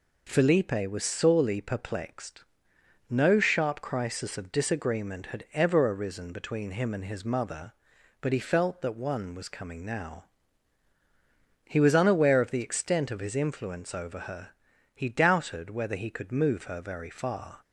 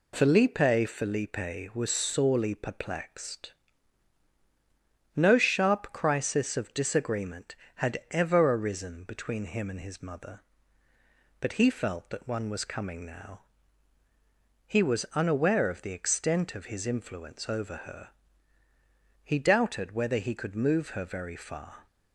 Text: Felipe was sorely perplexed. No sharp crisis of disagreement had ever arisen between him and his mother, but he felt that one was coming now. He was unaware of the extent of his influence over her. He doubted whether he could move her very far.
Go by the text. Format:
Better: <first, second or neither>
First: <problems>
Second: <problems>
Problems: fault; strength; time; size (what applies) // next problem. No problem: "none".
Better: first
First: none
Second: says "Felipe" twice; at 0.8 s